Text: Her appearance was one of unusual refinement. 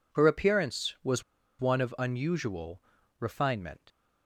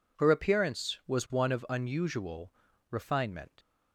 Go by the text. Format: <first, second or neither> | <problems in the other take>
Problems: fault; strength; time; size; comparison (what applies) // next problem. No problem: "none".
second | pauses between "was" and "one"; at 1.2 s; 0.36 s long // pauses between "unusual" and "refinement"; at 2.8 s; 0.38 s long; also in the second